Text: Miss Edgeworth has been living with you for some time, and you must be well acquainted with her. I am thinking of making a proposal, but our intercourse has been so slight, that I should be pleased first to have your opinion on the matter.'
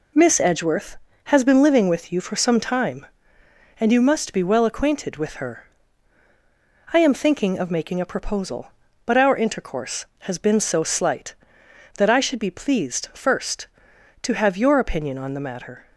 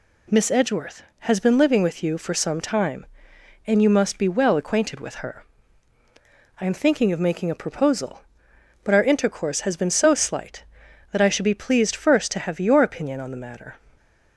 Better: neither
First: none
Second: none

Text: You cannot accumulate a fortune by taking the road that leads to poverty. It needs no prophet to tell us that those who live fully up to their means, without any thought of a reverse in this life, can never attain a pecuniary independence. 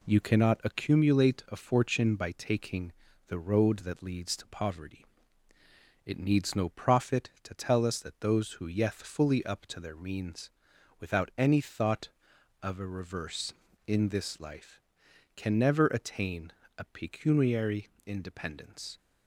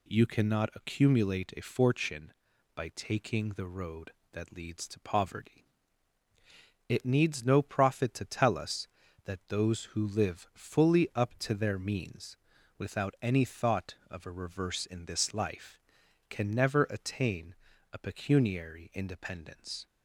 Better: second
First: pauses between "taking" and "the"; at 2.9 s; 0.38 s long // says "yeth" for "live"; at 8.6 s // pauses between "attain" and "a"; slight; at 16.5 s; 0.28 s long // pauses between "pecuniary" and "independence"; slight; at 17.8 s; 0.18 s long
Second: pauses between "attain" and "a"; slight; at 17.5 s; 0.36 s long

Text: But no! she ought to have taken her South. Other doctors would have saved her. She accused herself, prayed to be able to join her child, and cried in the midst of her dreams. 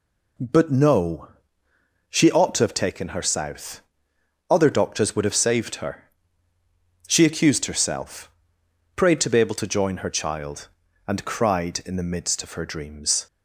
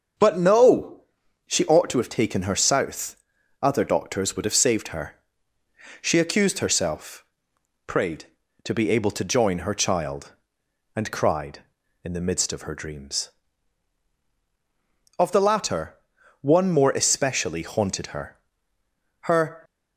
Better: first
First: none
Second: starts louder than the rest; until 1.6 s; 6 dB // goes on to say "Of the latter one more especially haunted her Her"; strong; from 15.1 s on; 4.4 s long

